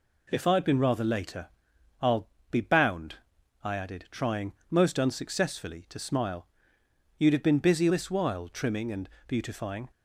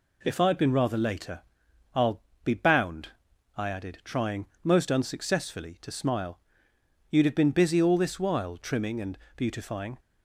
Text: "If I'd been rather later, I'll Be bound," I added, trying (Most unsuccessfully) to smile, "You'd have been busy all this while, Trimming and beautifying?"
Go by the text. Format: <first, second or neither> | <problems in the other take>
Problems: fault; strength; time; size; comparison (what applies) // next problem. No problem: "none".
second | pauses between "I'll" and "Be"; slight; at 2.2 s; 0.22 s long; slight in the second // skips "all"; at 7.8 s // pauses between "and" and "beautifying"; slight; at 9.0 s; 0.18 s long; slight in the second